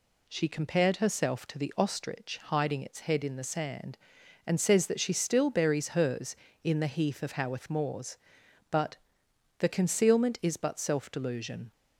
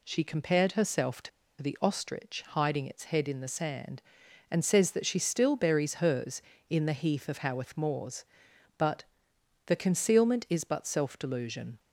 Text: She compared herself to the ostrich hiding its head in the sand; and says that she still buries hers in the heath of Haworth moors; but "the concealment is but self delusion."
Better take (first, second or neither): first